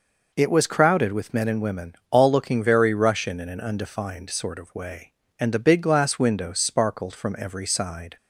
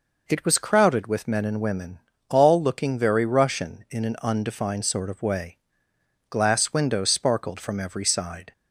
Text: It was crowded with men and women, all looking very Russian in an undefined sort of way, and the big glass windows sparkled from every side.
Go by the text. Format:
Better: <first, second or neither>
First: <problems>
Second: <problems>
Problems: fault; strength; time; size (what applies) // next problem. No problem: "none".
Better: first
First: none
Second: skips "and the big"; at 5.9 s